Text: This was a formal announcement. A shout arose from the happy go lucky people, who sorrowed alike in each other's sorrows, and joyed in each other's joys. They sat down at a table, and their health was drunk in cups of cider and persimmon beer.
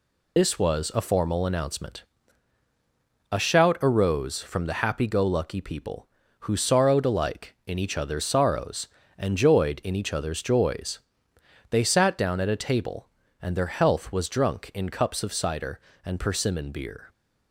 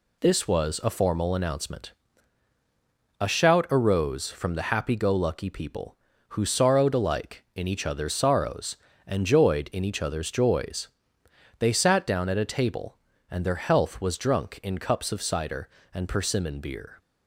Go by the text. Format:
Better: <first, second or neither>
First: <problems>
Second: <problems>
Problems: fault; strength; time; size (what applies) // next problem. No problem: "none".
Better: second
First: loses the start of "This"; at 0.3 s; 45 ms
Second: none